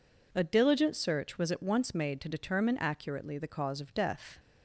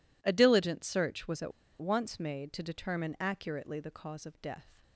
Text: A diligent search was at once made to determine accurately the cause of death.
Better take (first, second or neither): first